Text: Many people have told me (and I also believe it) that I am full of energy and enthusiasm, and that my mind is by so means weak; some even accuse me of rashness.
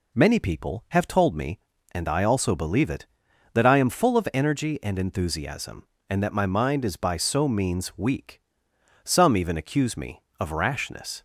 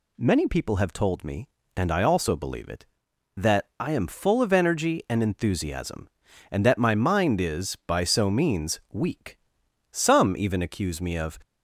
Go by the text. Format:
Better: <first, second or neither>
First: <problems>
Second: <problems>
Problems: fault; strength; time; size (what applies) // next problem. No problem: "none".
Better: first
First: none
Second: stops before "rashness"; at 11.4 s